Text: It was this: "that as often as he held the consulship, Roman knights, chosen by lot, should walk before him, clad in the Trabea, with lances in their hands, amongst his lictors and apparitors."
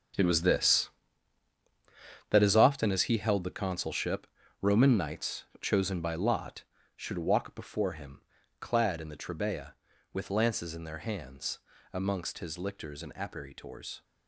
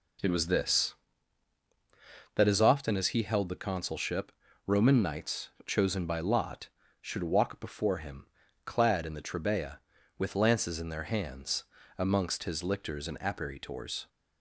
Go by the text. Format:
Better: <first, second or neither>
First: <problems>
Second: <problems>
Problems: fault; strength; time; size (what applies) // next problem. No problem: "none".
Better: second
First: gets quieter; strong; throughout; 12.5 dB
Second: none